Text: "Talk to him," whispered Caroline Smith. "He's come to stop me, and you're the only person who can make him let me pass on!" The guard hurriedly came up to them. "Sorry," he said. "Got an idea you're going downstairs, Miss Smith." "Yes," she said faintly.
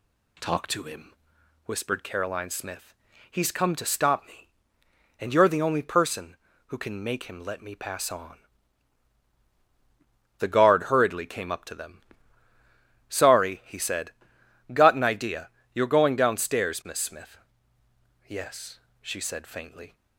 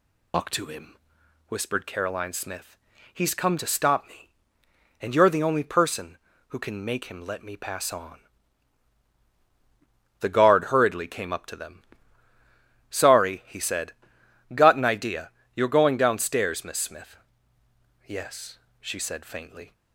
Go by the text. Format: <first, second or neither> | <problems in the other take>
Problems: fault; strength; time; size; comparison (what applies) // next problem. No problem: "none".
first | loses the start of "Talk"; at 0.3 s; 145 ms // pauses between "idea" and "you're"; slight; at 15.3 s; 0.24 s long; slight in the first